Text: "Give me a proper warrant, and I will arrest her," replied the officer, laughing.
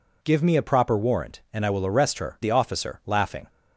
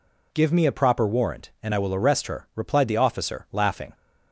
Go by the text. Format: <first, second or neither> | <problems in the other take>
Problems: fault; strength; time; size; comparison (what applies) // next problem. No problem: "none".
second | skips "replied"; at 2.3 s